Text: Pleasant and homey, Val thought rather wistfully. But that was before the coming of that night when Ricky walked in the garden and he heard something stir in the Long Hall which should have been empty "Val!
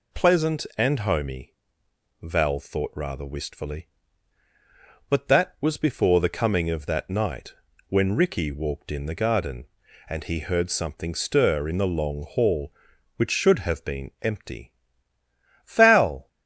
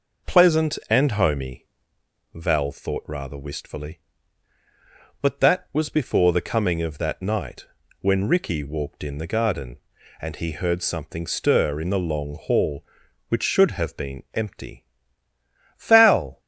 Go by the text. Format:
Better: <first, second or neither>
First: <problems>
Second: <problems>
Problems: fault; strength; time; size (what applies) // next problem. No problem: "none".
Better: first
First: pauses between "night" and "when"; slight; at 7.5 s; 0.34 s long // pauses between "empty" and "Val"; noticeable; at 14.7 s; 0.94 s long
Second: starts louder than the rest; noticeable; until 1.9 s; 5.5 dB // pauses between "night" and "when"; slight; at 7.6 s; 0.34 s long // pauses between "empty" and "Val"; noticeable; at 14.8 s; 0.94 s long